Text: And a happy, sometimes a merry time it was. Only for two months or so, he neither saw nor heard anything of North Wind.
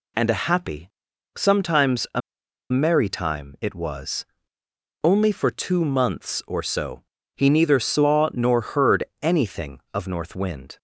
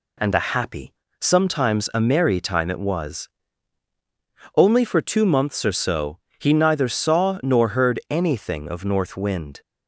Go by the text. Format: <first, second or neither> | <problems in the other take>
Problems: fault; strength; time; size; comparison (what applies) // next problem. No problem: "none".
second | pauses between "a" and "merry"; noticeable; at 2.2 s; 0.51 s long // pauses between "heard" and "anything"; slight; at 9.0 s; 0.18 s long